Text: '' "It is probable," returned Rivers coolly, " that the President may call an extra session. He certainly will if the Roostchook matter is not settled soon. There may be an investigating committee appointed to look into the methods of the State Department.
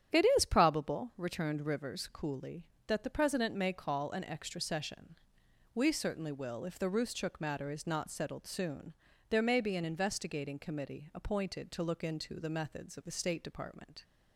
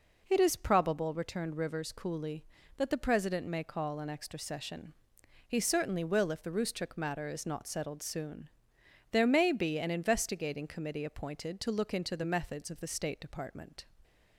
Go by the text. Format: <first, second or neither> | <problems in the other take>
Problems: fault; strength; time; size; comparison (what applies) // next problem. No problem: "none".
second | starts louder than the rest; strong; until 1.2 s; 9 dB // says "We" for "He"; at 5.7 s